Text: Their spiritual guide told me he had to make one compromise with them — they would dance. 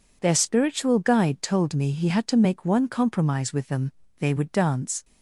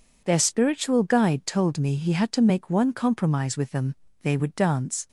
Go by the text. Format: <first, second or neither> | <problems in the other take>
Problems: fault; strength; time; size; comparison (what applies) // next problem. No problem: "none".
neither | none